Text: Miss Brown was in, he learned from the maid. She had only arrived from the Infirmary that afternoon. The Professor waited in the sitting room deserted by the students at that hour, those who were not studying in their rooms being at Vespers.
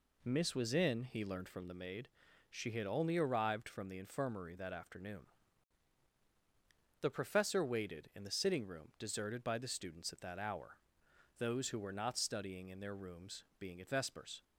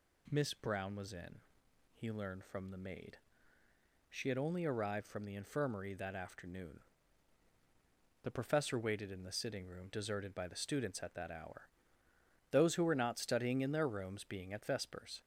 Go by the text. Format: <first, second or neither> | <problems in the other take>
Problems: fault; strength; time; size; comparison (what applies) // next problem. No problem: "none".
second | skips "Brown"; at 0.5 s